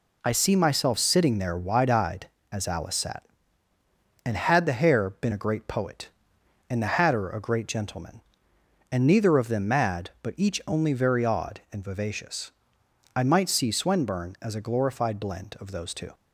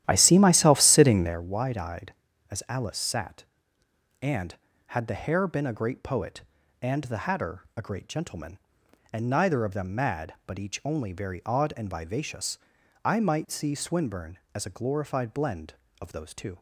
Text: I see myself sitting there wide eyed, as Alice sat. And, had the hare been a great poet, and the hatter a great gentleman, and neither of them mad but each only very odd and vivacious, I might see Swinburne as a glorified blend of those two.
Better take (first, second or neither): first